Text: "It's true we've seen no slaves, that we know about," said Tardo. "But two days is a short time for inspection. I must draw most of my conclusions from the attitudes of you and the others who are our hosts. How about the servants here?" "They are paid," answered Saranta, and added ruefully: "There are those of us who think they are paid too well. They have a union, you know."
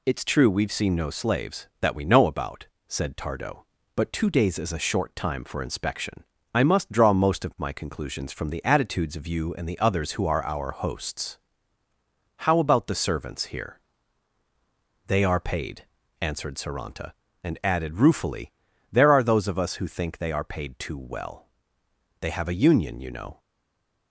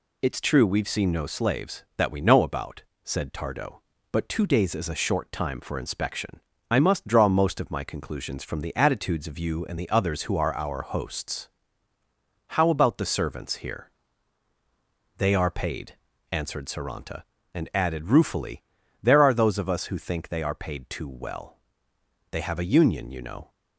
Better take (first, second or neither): second